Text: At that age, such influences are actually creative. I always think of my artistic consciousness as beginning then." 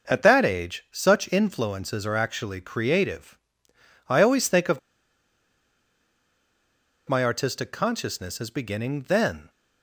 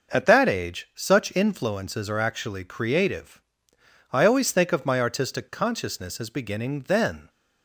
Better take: second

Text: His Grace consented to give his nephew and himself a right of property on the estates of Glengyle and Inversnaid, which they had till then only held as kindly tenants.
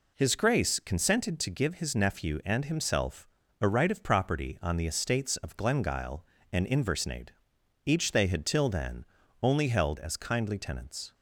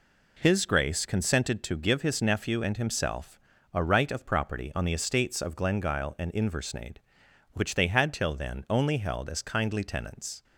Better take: second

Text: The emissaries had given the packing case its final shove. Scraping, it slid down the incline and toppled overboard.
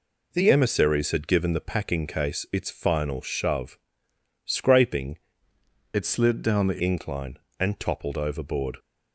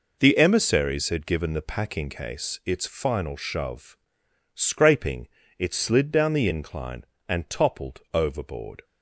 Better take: second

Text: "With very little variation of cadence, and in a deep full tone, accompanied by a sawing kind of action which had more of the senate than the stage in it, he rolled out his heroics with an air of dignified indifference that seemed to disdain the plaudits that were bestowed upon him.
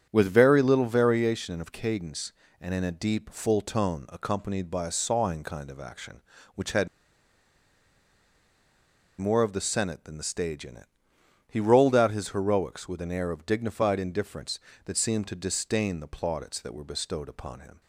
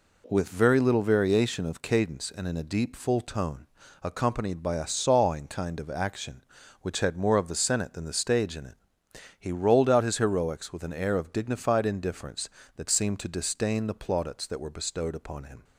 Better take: second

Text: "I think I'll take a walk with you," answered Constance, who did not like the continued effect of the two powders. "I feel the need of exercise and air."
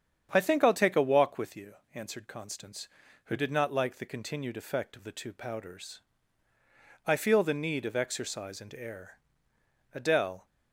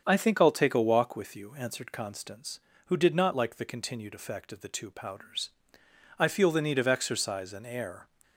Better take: second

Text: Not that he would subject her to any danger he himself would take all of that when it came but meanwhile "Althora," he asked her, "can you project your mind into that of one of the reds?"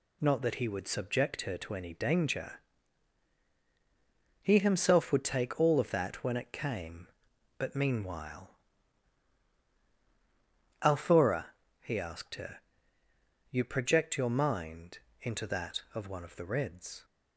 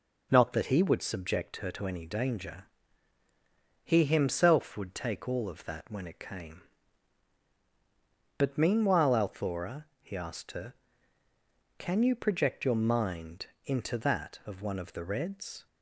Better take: second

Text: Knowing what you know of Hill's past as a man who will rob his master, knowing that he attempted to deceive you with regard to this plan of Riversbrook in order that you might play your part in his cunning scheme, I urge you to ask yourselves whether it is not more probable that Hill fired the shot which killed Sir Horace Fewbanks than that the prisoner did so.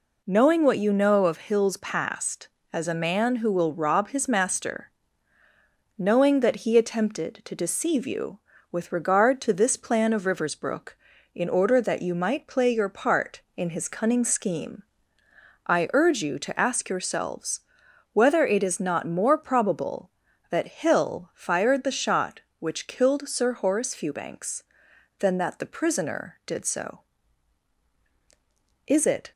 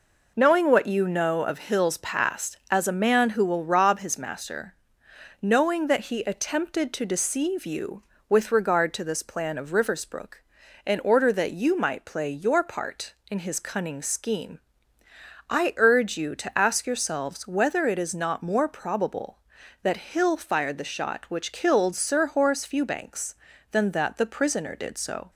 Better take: second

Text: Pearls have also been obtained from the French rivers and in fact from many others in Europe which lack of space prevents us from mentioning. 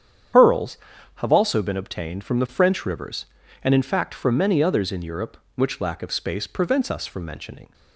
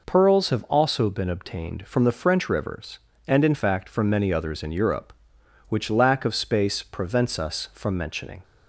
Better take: second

